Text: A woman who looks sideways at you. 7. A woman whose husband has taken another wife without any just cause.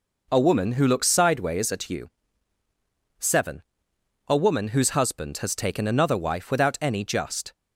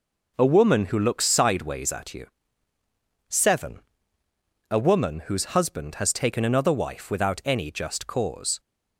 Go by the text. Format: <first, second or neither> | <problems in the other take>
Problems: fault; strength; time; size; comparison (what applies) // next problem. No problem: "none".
second | stops before "cause"; at 7.5 s